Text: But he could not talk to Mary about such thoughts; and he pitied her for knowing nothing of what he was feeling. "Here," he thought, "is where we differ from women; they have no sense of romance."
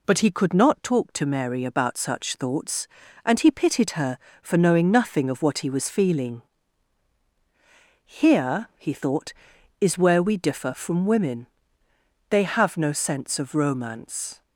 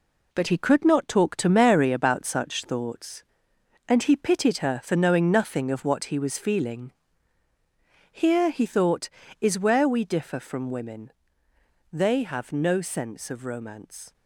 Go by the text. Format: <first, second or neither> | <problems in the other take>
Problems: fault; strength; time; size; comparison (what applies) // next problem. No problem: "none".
first | gets quieter; throughout; 7 dB